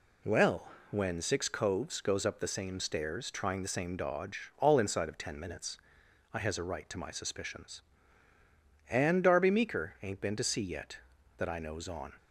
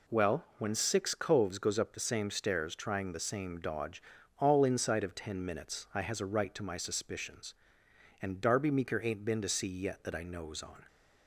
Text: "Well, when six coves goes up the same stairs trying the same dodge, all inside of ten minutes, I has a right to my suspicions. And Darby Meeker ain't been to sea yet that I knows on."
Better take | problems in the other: neither | none

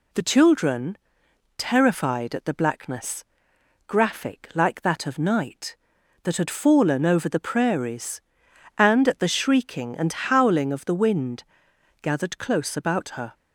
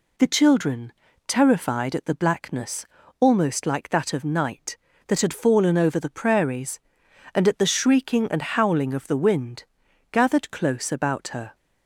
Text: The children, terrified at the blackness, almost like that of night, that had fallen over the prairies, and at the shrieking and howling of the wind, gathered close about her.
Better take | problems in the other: second | says "graphic" for "almost"; at 3.8 s

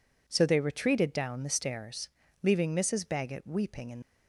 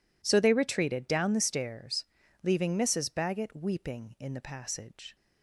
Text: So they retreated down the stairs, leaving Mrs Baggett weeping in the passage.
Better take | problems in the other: second | stops before "the passage"; at 4.0 s

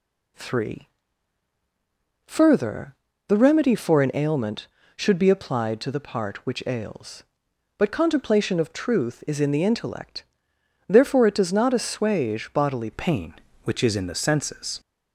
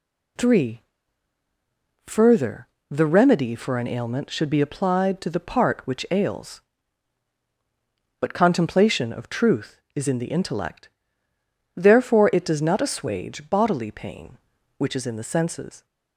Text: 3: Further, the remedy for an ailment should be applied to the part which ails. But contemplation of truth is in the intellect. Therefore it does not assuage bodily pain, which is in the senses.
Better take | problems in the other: second | changes voice at "pain"; from 12.9 s on; 1.8 s long

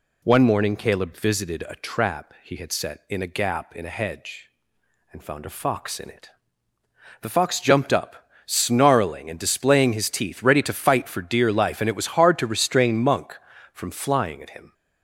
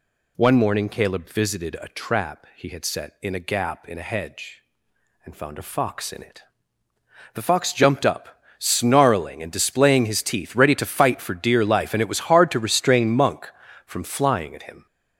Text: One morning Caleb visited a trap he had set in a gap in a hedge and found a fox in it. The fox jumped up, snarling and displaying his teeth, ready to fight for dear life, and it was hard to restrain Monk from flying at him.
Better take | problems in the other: first | gets louder; throughout; 6.5 dB

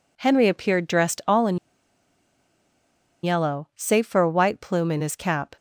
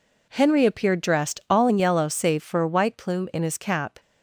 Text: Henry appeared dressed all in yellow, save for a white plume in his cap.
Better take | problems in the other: second | pauses between "in" and "yellow"; strong; at 1.5 s; 1.6 s long

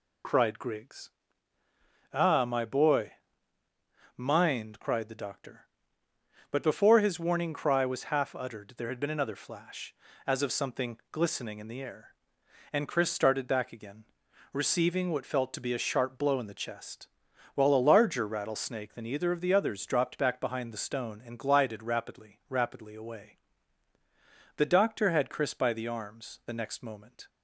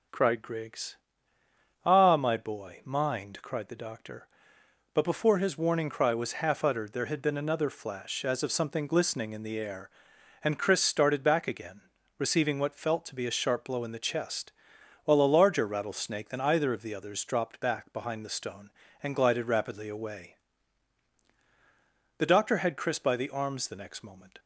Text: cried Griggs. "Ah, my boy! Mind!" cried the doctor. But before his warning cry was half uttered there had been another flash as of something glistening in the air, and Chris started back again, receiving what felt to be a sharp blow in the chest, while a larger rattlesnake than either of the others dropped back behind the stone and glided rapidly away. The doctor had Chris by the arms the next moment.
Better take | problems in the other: second | says "rapidly" twice; at 22.4 s

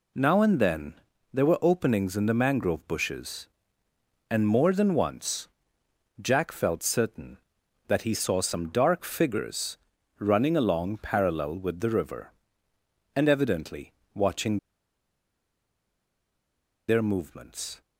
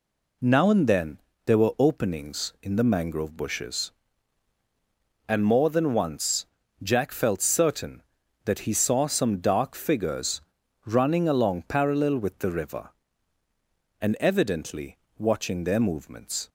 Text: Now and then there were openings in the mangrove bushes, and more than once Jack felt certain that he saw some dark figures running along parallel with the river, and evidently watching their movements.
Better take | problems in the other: second | pauses between "then" and "there"; at 0.9 s; 0.38 s long; slight in the second // pauses between "once" and "Jack"; noticeable; at 5.4 s; 0.72 s long; also in the second // pauses between "figures" and "running"; at 9.7 s; 0.40 s long; also in the second // pauses between "evidently" and "watching"; slight; at 13.9 s; 0.24 s long; slight in the second // pauses between "watching" and "their"; strong; at 14.5 s; 2.3 s long

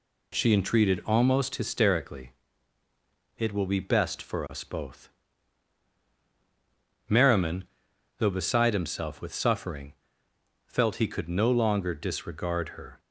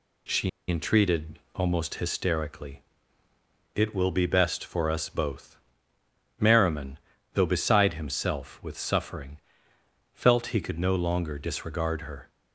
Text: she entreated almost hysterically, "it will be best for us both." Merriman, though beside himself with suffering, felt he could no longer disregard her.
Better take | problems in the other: first | pauses between "she" and "entreated"; slight; at 0.4 s; 0.19 s long // pauses between "entreated" and "almost"; slight; at 1.3 s; 0.16 s long

